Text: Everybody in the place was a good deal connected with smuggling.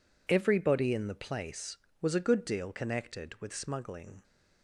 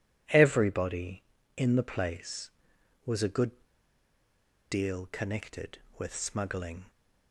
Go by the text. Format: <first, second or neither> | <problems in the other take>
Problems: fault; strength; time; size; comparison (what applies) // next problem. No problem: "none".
first | pauses between "good" and "deal"; at 3.5 s; 1.1 s long